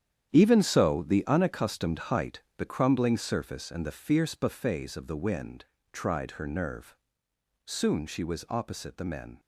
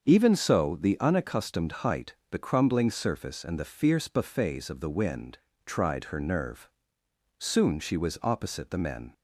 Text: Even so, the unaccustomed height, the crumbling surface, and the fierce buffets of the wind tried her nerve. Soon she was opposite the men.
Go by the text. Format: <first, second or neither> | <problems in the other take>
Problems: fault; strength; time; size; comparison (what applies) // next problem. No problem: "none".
second | gets quieter; strong; throughout; 11.5 dB // starts louder than the rest; strong; until 1.3 s; 9.5 dB; also in the second // pauses between "wind" and "tried"; slight; at 5.6 s; 0.26 s long; slight in the second